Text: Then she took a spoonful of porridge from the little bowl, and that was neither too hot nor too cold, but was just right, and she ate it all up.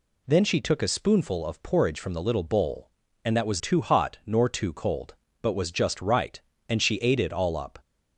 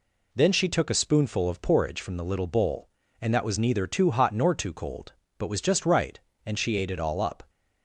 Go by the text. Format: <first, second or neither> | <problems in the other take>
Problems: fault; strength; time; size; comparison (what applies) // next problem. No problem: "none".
second | skips "neither"; at 3.5 s